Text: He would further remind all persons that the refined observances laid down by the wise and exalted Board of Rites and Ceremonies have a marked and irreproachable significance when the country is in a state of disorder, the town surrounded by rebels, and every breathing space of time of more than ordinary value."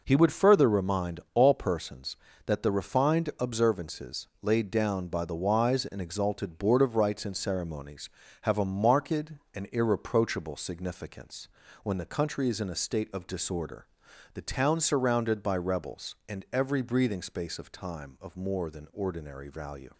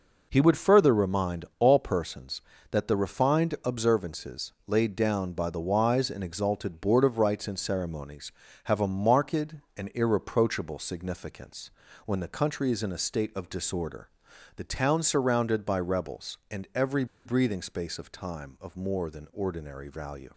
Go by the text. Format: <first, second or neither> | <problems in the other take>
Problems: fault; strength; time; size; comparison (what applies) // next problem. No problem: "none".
first | pauses between "significance" and "when"; slight; at 11.7 s; 0.34 s long; slight in the first // pauses between "every" and "breathing"; slight; at 17.0 s; 0.20 s long